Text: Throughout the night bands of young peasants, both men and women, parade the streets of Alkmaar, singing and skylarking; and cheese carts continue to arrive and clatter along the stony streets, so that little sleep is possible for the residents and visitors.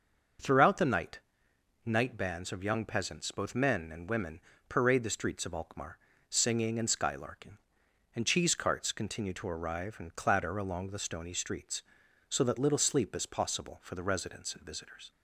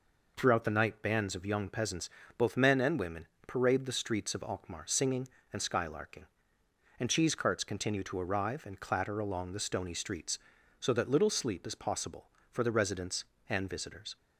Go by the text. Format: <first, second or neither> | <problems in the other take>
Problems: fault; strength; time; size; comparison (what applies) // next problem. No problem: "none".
second | starts louder than the rest; until 2.0 s; 6.5 dB // says "night" twice; at 1.8 s